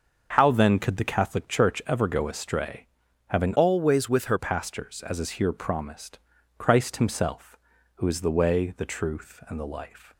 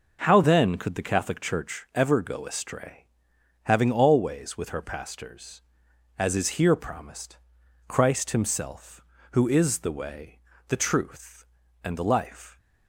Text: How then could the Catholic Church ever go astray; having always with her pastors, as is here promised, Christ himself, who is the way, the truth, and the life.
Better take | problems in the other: second | starts louder than the rest; until 1.3 s; 6 dB // changes voice from "always" to "her"; from 3.5 to 4.3 s; 0.8 s long

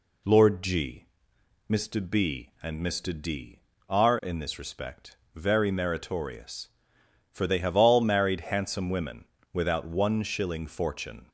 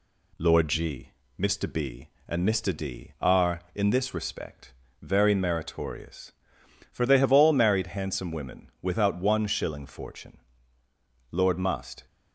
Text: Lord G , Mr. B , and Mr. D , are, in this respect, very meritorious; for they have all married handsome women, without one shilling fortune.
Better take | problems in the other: first | goes on to say "Lord must"; noticeable; from 11.2 s on; 0.76 s long

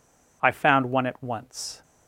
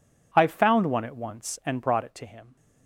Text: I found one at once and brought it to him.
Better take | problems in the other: second | stops before "and brought it to him"; at 1.8 s

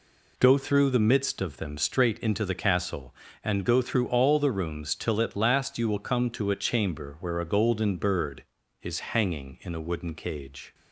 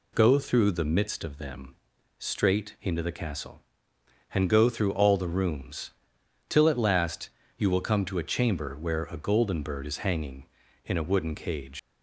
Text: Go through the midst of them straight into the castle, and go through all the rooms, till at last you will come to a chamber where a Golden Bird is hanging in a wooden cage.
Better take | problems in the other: first | pauses between "them" and "straight"; noticeable; at 1.7 s; 0.46 s long // pauses between "last" and "you"; slight; at 7.2 s; 0.28 s long // leaves "cage" unfinished; at 11.7 s; 130 ms

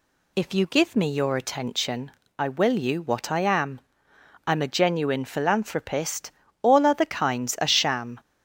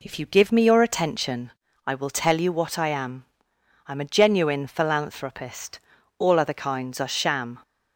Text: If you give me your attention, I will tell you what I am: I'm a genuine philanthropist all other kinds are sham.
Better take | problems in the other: second | skips "tell"; at 2.7 s // pauses between "philanthropist" and "all"; slight; at 6.3 s; 0.32 s long; also in the second

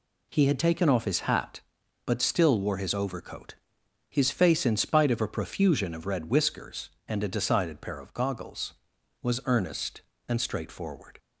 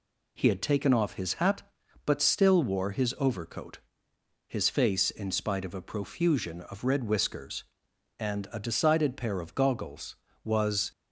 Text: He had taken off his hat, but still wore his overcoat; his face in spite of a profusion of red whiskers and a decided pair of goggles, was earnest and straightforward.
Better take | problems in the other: first | stops before "earnest and straightforward"; at 10.9 s

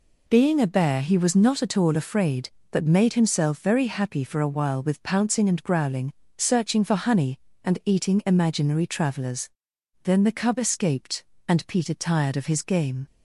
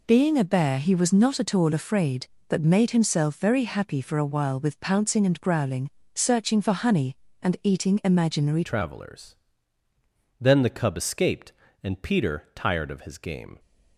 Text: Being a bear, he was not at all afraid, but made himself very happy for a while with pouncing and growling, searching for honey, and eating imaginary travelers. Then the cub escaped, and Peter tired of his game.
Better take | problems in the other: first | changes voice at "travelers"; from 8.6 s on; 4.9 s long

